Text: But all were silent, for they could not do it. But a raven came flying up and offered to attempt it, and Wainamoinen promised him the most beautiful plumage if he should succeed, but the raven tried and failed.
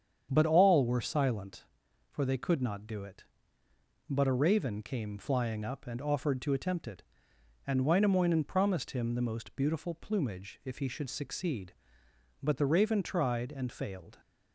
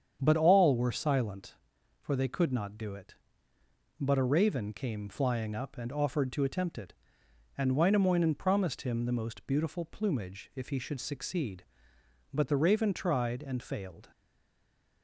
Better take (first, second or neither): first